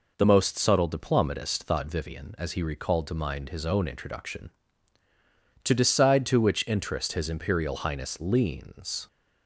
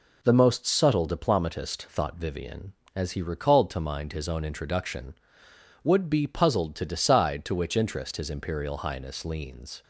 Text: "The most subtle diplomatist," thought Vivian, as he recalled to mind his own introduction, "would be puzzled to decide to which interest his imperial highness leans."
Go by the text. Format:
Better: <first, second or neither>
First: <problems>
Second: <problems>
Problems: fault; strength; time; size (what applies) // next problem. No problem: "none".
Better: second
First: skips "would be puzzled"; at 5.0 s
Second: none